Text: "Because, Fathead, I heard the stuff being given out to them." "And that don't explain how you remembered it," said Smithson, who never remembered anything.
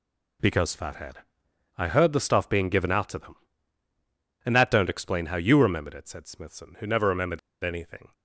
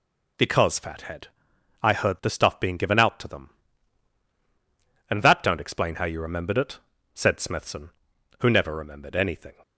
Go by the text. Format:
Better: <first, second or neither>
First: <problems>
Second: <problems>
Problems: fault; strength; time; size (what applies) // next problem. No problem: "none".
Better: second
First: pauses between "remembered" and "anything"; slight; at 7.3 s; 0.24 s long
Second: none